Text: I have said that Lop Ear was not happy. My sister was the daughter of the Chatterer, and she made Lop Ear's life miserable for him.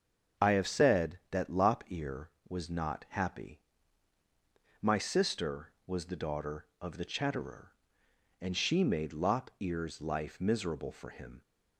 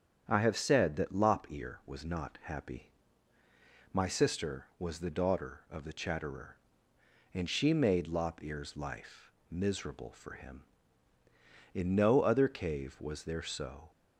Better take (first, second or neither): first